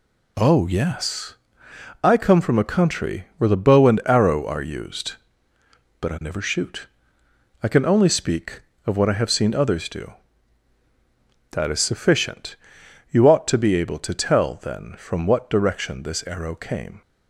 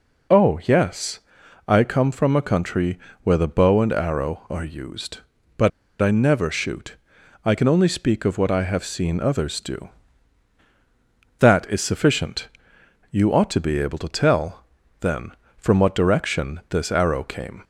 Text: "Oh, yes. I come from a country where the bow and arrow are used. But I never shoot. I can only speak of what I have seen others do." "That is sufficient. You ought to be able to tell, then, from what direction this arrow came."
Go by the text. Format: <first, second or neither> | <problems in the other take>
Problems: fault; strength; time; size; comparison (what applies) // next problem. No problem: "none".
first | pauses between "country" and "where"; slight; at 2.9 s; 0.24 s long // pauses between "But" and "I"; slight; at 5.7 s; 0.31 s long